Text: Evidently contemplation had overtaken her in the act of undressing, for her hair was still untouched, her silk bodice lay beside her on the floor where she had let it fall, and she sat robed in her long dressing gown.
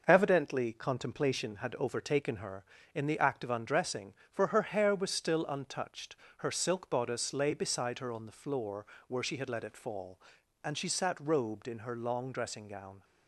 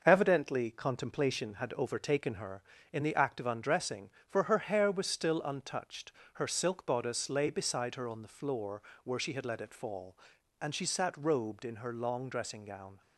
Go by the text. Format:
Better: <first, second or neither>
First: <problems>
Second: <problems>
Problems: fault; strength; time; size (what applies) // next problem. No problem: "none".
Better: neither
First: pauses between "floor" and "where"; slight; at 8.8 s; 0.22 s long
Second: pauses between "floor" and "where"; slight; at 8.8 s; 0.22 s long